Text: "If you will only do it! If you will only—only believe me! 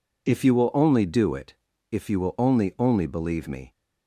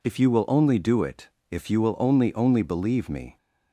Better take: neither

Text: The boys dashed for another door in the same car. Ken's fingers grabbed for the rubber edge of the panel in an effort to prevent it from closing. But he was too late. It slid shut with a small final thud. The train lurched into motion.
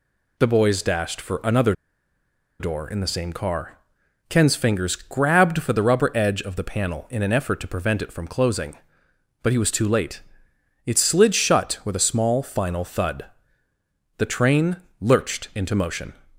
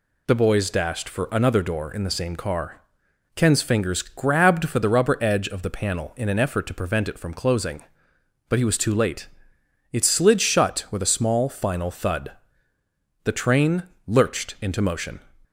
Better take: second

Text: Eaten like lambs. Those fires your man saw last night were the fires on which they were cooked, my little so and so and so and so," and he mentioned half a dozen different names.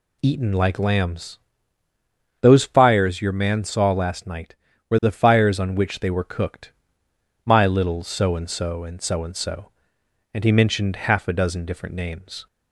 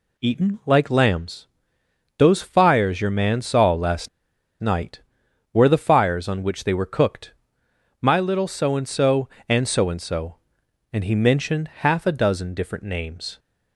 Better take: first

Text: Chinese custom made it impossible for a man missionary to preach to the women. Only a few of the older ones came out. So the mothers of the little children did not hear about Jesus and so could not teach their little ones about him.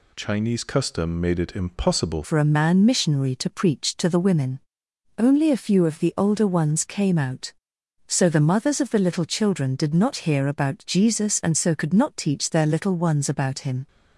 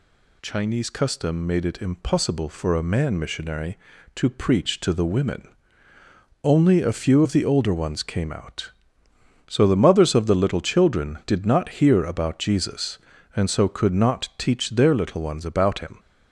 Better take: second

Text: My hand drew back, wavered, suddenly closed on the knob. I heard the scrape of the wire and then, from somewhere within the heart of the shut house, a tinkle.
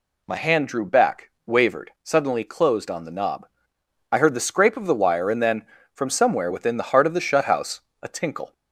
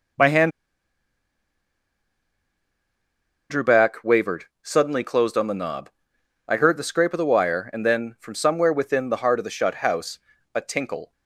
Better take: first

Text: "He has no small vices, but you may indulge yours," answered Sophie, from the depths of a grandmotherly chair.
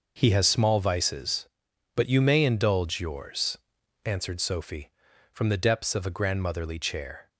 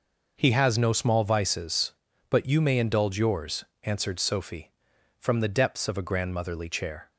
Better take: second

